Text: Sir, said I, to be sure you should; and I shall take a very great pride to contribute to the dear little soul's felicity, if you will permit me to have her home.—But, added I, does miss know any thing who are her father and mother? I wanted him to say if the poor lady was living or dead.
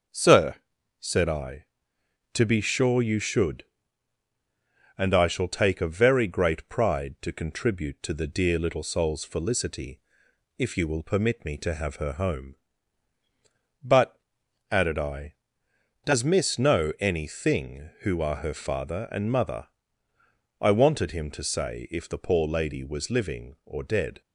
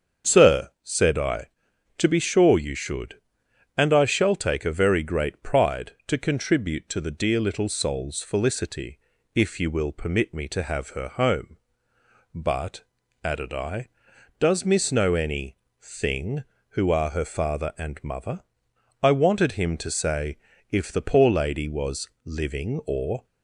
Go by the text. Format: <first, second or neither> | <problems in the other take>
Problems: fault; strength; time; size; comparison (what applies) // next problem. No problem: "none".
first | starts louder than the rest; strong; until 1.3 s; 7 dB; noticeable in the first // pauses between "any" and "thing"; slight; at 15.5 s; 0.22 s long // pauses between "say" and "if"; slight; at 20.3 s; 0.34 s long // stops before "dead"; at 23.2 s